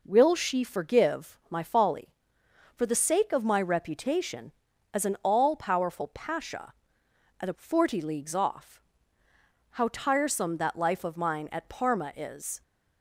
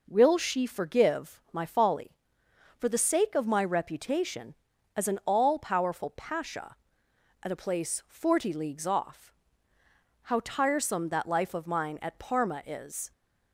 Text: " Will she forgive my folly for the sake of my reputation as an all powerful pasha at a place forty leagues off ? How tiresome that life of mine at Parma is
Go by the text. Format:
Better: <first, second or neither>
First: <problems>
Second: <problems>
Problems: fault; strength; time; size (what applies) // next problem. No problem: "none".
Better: second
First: skips "place"; at 7.5 s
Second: none